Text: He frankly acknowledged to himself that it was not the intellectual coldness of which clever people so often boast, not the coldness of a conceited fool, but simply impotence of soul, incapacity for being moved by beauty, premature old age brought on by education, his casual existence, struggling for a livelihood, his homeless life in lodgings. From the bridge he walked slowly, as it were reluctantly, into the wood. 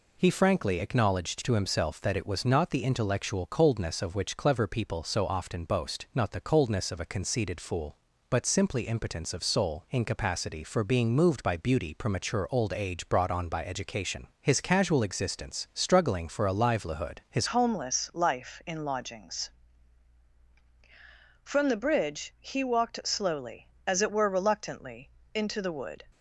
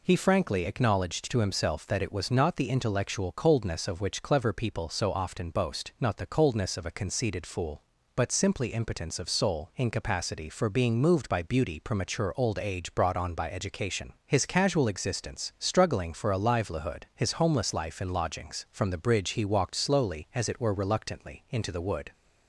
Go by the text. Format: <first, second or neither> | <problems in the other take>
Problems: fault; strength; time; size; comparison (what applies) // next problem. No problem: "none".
second | changes voice at "homeless"; from 17.4 s on; 8.6 s long